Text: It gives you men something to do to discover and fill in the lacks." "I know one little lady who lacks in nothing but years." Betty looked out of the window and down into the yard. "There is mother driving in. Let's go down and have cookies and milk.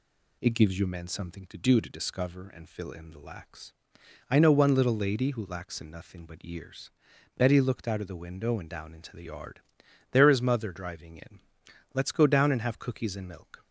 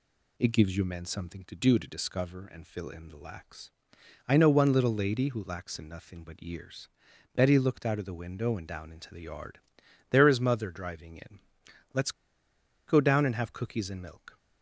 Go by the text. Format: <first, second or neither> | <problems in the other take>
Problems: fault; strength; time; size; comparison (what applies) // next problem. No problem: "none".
first | pauses between "Let's" and "go"; noticeable; at 12.1 s; 0.76 s long